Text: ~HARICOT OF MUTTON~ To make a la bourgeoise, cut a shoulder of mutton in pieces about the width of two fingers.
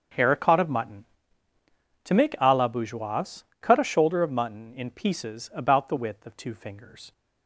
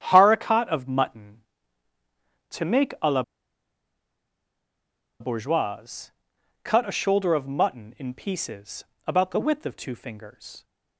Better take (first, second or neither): first